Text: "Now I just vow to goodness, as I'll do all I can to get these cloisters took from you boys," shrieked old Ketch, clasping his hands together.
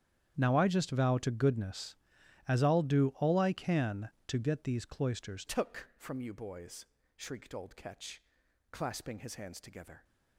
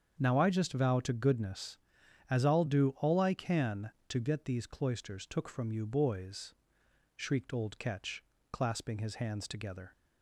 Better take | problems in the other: second | starts louder than the rest; strong; until 1.3 s; 9.5 dB; strong in the second // changes voice at "took"; from 5.4 s on; 4.6 s long

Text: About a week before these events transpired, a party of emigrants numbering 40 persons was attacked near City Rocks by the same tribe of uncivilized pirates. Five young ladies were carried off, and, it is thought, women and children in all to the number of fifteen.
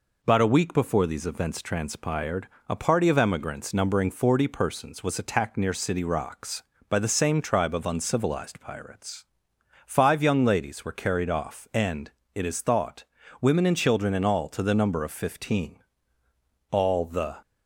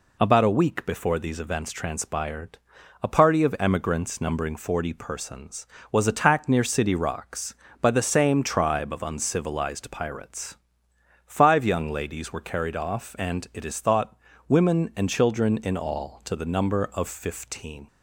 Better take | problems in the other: second | goes on to say "All the"; noticeable; from 16.6 s on; 0.70 s long

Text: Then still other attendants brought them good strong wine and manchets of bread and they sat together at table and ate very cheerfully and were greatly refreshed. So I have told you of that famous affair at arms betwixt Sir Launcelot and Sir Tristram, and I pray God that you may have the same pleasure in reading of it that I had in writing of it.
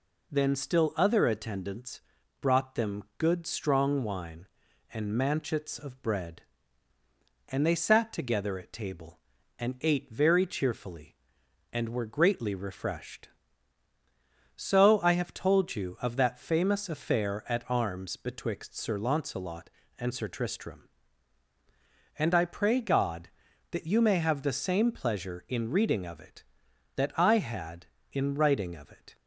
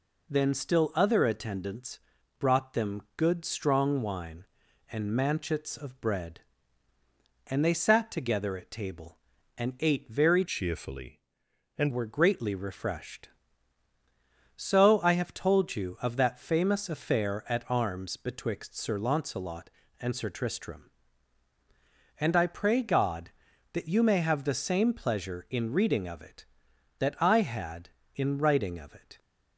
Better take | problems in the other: first | pauses between "attendants" and "brought"; at 1.9 s; 0.40 s long; also in the first // changes voice from "cheerfully" to "and"; from 10.4 to 11.9 s; 1.5 s long

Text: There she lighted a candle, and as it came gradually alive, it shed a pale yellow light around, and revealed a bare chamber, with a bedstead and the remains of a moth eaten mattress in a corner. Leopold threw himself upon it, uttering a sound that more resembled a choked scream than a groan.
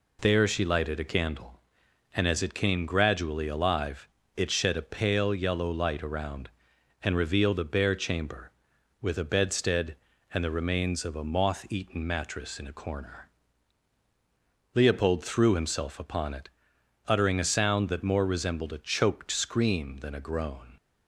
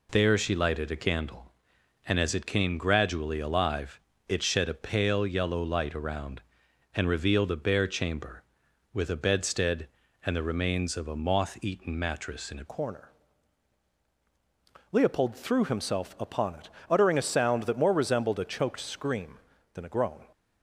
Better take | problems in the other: first | changes voice at "corner"; from 12.6 s on; 7.6 s long

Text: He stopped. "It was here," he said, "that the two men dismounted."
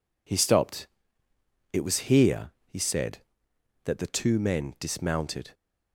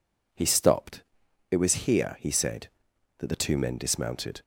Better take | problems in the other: neither | none

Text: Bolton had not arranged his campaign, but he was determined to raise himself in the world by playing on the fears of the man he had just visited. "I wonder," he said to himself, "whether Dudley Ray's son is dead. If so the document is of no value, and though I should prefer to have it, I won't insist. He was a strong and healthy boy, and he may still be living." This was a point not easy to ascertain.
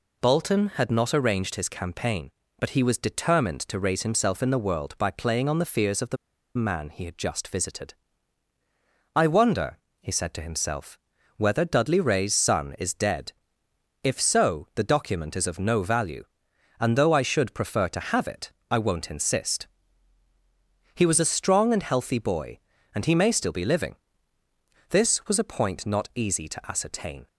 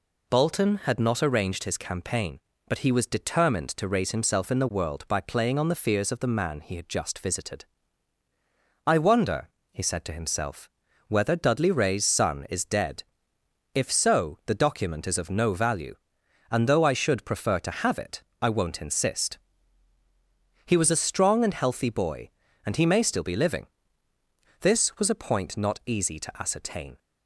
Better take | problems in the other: second | pauses between "the" and "man"; at 6.1 s; 0.39 s long

